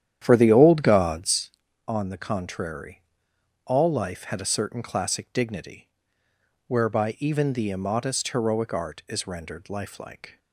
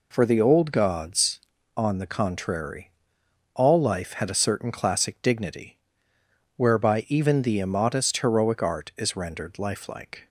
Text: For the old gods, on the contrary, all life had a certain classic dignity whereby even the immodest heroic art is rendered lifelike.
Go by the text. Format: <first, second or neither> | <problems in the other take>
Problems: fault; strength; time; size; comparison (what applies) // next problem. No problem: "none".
second | starts louder than the rest; strong; until 1.4 s; 10 dB // pauses between "dignity" and "whereby"; noticeable; at 5.8 s; 0.80 s long; noticeable in the second